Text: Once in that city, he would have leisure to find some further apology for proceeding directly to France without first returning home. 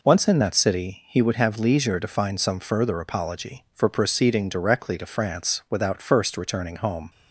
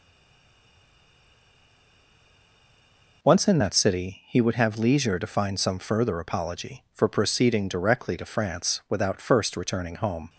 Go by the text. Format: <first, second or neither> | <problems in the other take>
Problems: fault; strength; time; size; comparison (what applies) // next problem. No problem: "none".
first | stays silent before the first word; strong; until 3.2 s; 3.2 s long